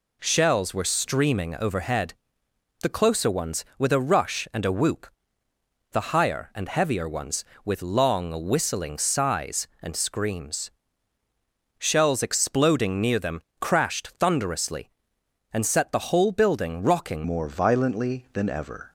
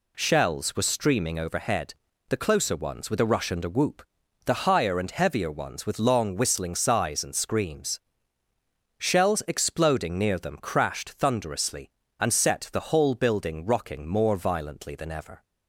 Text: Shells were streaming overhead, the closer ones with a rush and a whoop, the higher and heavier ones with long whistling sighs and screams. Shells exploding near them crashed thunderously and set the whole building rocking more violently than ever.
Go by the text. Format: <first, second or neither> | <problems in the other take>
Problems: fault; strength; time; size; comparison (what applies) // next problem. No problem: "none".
second | pauses between "them" and "crashed"; slight; at 13.4 s; 0.20 s long // changes voice at "more"; from 17.2 s on; 1.7 s long